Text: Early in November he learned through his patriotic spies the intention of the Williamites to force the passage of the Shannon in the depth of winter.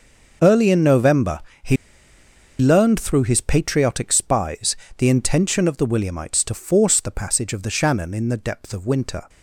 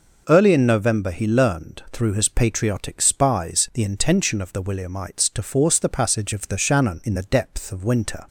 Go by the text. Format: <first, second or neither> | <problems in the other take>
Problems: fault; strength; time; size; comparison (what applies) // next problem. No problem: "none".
second | pauses between "November" and "he"; slight; at 1.3 s; 0.24 s long // pauses between "he" and "learned"; noticeable; at 1.7 s; 0.84 s long // pauses between "spies" and "the"; slight; at 4.7 s; 0.22 s long